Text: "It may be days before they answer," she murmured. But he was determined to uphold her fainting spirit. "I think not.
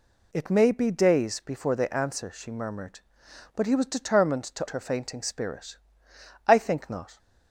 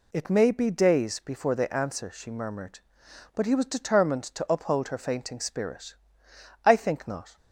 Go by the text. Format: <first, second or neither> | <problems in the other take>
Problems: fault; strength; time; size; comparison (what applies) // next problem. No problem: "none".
second | skips "uphold"; at 4.6 s